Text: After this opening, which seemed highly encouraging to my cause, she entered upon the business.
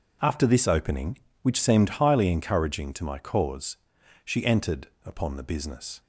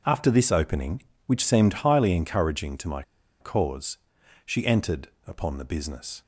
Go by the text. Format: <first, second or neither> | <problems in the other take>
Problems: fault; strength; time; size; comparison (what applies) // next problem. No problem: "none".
first | pauses between "my" and "cause"; at 3.0 s; 0.38 s long // pauses between "entered" and "upon"; slight; at 5.0 s; 0.20 s long; slight in the first